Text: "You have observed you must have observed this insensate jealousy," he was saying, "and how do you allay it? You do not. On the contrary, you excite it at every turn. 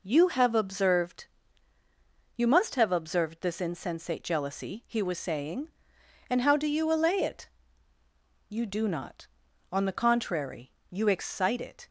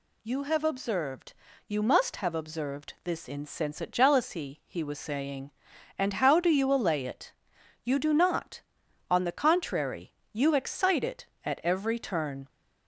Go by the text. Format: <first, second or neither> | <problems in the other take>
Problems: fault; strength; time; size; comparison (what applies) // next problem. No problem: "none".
second | pauses between "observed" and "you"; at 1.2 s; 1.1 s long; slight in the second // stops before "at every turn"; at 11.8 s